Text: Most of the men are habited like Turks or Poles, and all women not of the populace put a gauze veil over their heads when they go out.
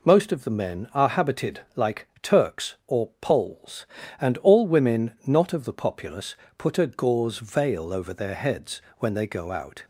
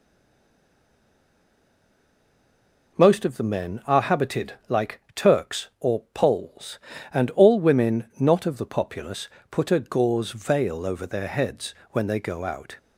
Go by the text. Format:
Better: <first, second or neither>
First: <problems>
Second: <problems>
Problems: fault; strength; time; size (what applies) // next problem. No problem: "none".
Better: first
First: pauses between "like" and "Turks"; slight; at 2.0 s; 0.16 s long // pauses between "populace" and "put"; slight; at 6.3 s; 0.22 s long // pauses between "heads" and "when"; slight; at 8.8 s; 0.16 s long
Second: stays silent before the first word; strong; until 2.9 s; 2.9 s long // pauses between "like" and "Turks"; slight; at 4.9 s; 0.16 s long // pauses between "populace" and "put"; slight; at 9.2 s; 0.22 s long // pauses between "heads" and "when"; slight; at 11.7 s; 0.16 s long